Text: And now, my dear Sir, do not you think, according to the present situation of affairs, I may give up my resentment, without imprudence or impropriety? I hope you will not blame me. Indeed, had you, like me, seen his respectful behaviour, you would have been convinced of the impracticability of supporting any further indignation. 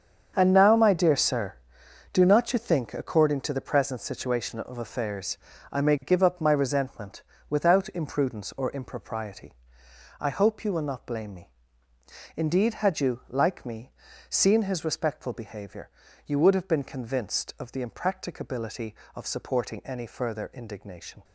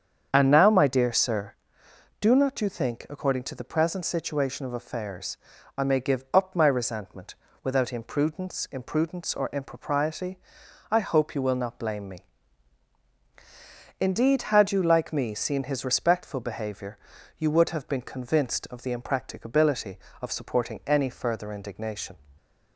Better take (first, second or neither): first